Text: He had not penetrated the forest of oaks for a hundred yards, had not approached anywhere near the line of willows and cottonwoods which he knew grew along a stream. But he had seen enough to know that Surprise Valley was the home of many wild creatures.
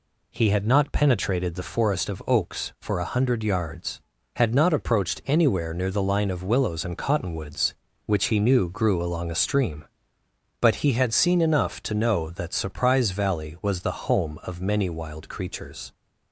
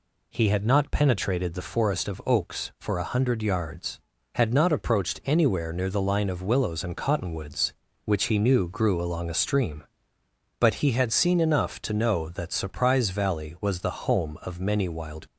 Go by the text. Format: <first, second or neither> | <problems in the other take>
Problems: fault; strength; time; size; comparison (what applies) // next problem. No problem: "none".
first | stops before "creatures"; at 15.2 s